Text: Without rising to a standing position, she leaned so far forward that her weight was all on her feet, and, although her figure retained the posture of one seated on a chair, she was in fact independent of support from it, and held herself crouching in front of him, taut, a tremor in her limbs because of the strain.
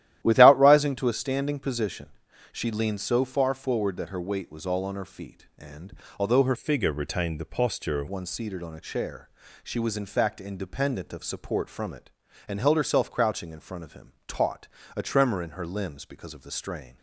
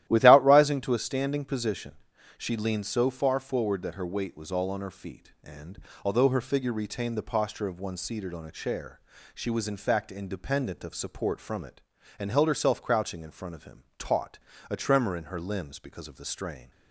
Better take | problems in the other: second | starts louder than the rest; strong; until 1.2 s; 13 dB; strong in the second // changes voice from "figure" to "of"; from 6.5 to 8.0 s; 1.5 s long

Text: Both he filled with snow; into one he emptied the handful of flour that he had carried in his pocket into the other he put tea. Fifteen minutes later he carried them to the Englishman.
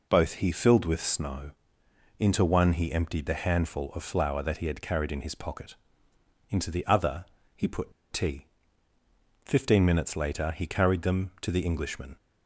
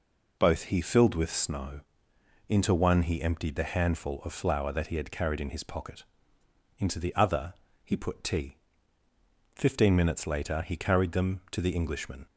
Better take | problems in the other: second | pauses between "pocket" and "into"; noticeable; at 5.7 s; 0.74 s long; noticeable in the second // pauses between "other" and "he"; slight; at 7.2 s; 0.30 s long; slight in the second // pauses between "put" and "tea"; slight; at 7.9 s; 0.19 s long

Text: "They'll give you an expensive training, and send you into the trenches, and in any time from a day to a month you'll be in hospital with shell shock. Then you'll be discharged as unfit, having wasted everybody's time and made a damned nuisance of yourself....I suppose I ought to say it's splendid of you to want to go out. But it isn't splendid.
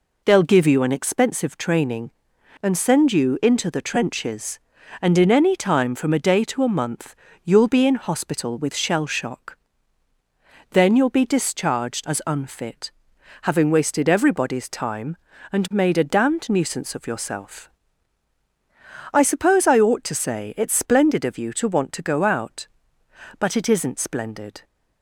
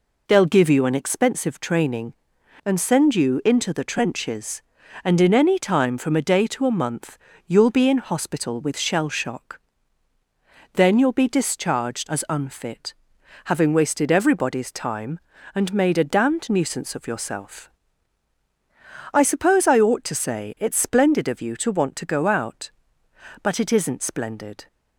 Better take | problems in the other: neither | pauses between "month" and "you'll"; slight; the same in both

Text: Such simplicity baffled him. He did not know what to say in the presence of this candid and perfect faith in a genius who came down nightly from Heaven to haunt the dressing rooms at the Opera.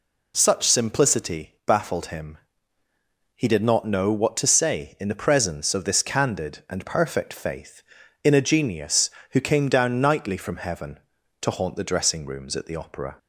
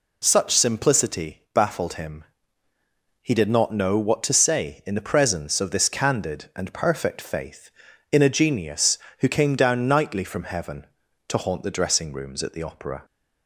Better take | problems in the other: neither | none

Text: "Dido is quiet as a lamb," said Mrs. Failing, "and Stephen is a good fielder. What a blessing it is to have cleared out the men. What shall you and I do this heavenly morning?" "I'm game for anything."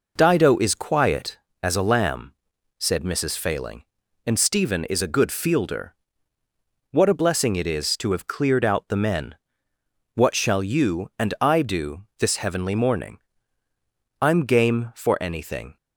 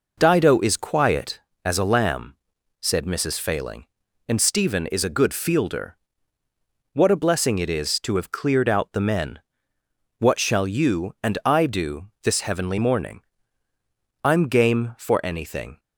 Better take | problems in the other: neither | pauses between "do" and "this"; slight; the same in both

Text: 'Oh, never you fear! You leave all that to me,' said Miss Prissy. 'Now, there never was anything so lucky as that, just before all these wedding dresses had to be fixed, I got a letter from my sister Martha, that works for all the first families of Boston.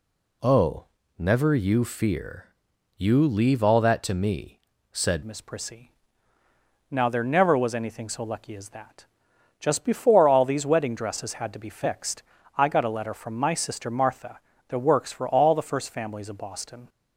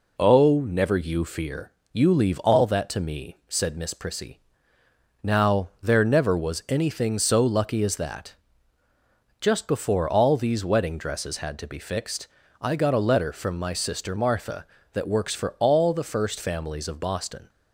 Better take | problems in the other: second | changes voice at "Miss"; from 5.2 s on; 11.6 s long

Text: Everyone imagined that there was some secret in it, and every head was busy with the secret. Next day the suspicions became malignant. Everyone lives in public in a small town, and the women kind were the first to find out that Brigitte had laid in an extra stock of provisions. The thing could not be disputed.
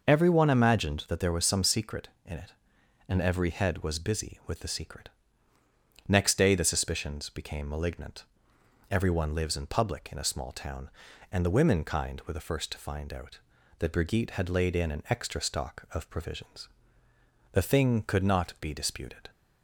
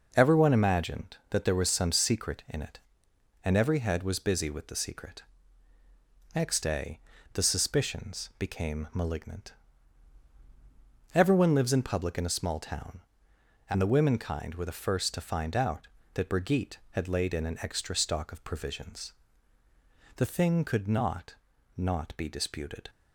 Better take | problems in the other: first | pauses between "day" and "the"; slight; at 6.9 s; 0.36 s long // says "not" twice; at 21.7 s

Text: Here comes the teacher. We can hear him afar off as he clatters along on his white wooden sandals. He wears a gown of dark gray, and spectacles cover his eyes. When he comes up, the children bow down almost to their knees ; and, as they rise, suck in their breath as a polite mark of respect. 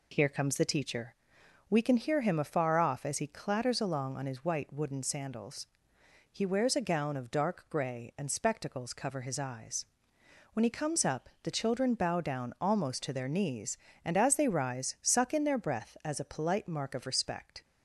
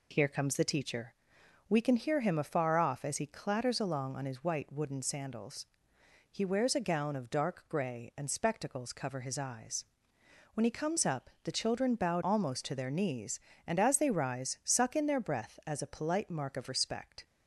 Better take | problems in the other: first | skips "down"; at 12.2 s

